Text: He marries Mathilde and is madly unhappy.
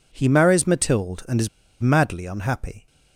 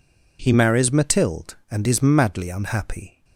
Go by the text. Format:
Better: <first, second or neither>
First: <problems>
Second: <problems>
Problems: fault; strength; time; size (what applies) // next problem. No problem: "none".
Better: second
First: pauses between "is" and "madly"; slight; at 1.4 s; 0.31 s long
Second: none